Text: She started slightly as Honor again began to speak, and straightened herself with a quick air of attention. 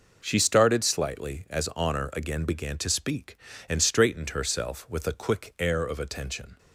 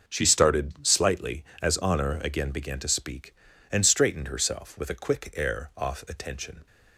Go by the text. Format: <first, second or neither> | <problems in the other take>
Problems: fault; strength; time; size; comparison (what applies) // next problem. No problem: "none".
first | says "off" for "of"; at 5.7 s